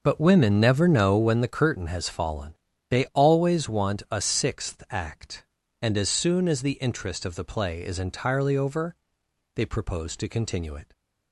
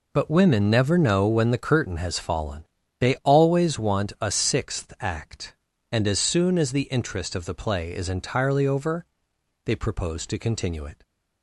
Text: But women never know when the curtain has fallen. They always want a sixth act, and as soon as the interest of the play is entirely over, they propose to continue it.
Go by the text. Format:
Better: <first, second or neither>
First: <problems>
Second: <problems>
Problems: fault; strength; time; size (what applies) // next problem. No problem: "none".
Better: second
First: starts louder than the rest; noticeable; until 1.4 s; 6 dB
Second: none